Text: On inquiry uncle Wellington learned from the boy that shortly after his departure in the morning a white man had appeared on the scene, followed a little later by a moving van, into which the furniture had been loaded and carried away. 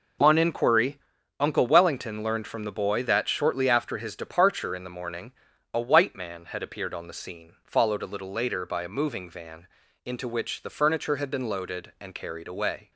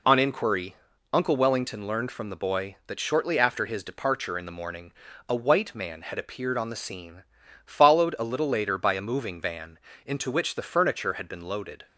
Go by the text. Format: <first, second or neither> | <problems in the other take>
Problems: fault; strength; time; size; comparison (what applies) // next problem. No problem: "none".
first | pauses between "inquiry" and "uncle"; at 0.7 s; 0.38 s long; also in the first // pauses between "morning" and "a"; at 4.9 s; 0.38 s long; also in the first // stops before "and carried away"; at 11.8 s